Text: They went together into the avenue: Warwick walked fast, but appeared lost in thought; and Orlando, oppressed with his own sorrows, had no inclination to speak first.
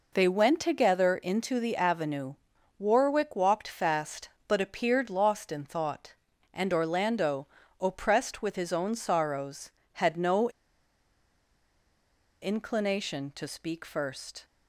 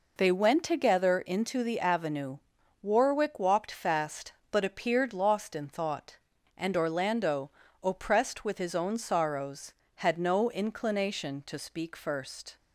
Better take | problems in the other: second | pauses between "no" and "inclination"; strong; at 10.4 s; 1.9 s long

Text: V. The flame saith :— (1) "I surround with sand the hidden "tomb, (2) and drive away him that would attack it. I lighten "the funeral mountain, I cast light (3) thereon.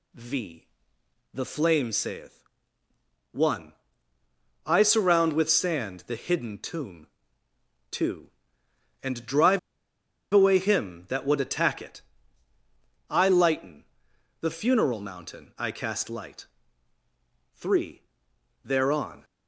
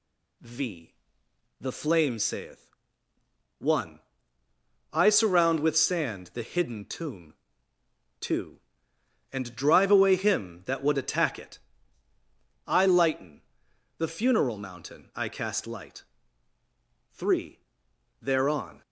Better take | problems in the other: second | pauses between "drive" and "away"; noticeable; at 9.5 s; 0.74 s long // pauses between "lighten" and "the"; noticeable; at 13.8 s; 0.56 s long; noticeable in the second

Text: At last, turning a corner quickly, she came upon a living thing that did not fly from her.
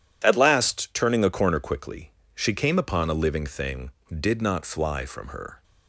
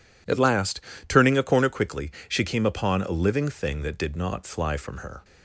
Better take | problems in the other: second | skips "that"; at 4.0 s

